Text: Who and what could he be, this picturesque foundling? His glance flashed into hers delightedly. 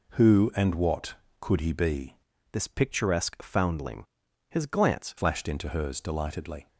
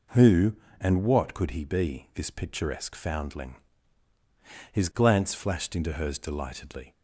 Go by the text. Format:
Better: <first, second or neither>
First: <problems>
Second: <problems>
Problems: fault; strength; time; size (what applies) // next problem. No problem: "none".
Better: second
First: changes voice from "this" to "glance"; from 2.5 to 5.1 s; 2.6 s long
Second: none